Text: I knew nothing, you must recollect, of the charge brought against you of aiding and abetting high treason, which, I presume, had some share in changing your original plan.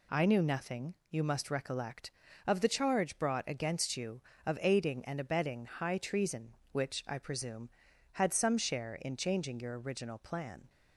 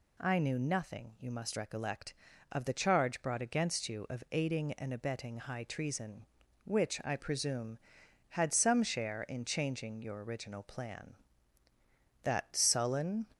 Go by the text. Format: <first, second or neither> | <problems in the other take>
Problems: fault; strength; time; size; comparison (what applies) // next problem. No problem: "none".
first | goes on to say "That sullen"; noticeable; from 12.2 s on; 1.0 s long